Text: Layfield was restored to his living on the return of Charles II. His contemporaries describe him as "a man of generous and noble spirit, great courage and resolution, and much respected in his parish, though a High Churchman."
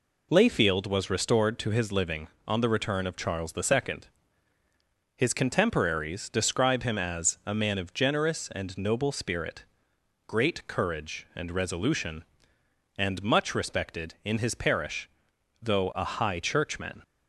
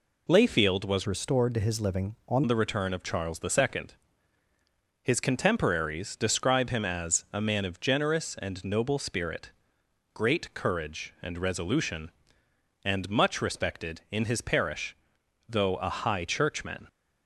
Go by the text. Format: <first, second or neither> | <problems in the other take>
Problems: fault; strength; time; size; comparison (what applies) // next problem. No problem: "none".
first | changes voice from "restored" to "on"; from 1.0 to 2.4 s; 1.4 s long